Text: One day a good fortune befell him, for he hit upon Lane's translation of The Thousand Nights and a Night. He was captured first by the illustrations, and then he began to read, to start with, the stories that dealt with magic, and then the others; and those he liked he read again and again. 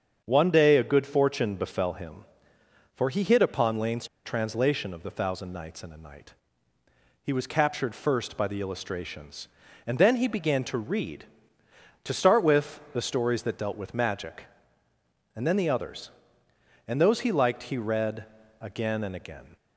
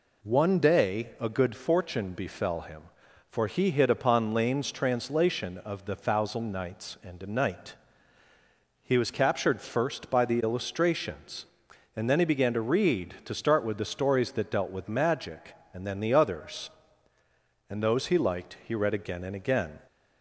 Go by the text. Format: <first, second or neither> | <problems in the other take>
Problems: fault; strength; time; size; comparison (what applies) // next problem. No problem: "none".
second | starts louder than the rest; strong; until 1.2 s; 7 dB // pauses between "Lane's" and "translation"; slight; at 4.0 s; 0.18 s long // pauses between "read" and "again"; at 18.2 s; 0.38 s long